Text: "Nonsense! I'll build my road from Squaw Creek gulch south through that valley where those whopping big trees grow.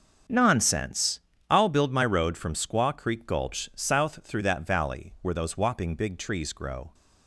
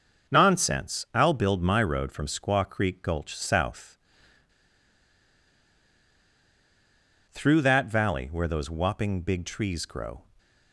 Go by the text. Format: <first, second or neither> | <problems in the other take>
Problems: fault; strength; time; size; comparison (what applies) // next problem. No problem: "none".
first | starts louder than the rest; until 1.3 s; 6.5 dB; also in the first // pauses between "south" and "through"; strong; at 3.9 s; 3.3 s long